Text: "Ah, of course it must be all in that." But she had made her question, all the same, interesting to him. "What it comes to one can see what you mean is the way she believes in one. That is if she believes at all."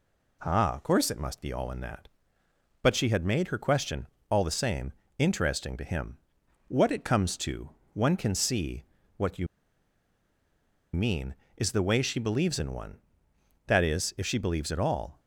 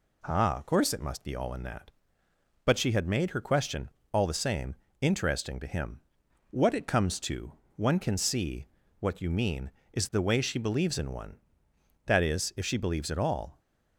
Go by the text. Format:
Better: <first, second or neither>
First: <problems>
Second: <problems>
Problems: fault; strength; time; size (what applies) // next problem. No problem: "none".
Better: second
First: pauses between "to" and "one"; slight; at 7.7 s; 0.22 s long // pauses between "see" and "what"; slight; at 8.8 s; 0.32 s long // pauses between "you" and "mean"; strong; at 9.4 s; 1.4 s long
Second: pauses between "to" and "one"; slight; at 7.5 s; 0.22 s long // pauses between "see" and "what"; slight; at 8.6 s; 0.32 s long